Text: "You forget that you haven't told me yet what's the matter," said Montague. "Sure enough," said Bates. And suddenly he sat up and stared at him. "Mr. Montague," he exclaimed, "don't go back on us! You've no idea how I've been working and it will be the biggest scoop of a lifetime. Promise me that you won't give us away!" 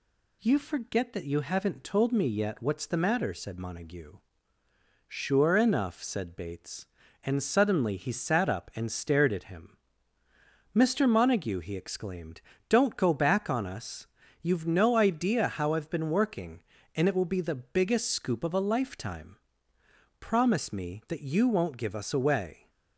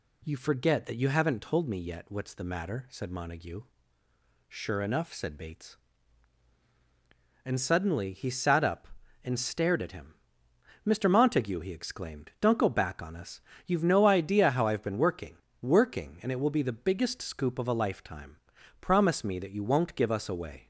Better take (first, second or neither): first